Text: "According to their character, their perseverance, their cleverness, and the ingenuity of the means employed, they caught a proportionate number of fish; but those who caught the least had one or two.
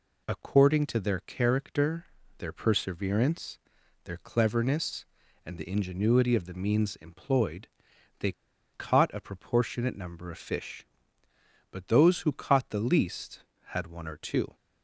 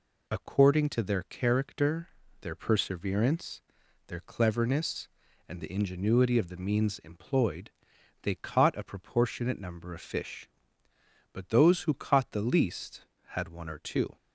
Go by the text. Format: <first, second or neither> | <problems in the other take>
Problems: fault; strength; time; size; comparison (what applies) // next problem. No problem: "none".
second | pauses between "they" and "caught"; at 8.3 s; 0.41 s long